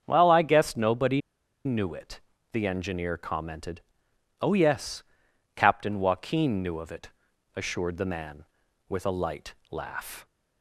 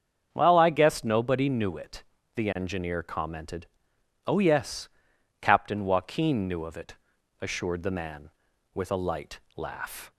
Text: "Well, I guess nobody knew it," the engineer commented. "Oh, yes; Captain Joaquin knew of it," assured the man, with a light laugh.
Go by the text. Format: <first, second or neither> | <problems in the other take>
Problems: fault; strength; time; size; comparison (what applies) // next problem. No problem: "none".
second | starts louder than the rest; strong; until 1.0 s; 7.5 dB; strong in the second // pauses between "nobody" and "knew"; at 1.2 s; 0.44 s long // pauses between "light" and "laugh"; slight; at 9.5 s; 0.16 s long; slight in the second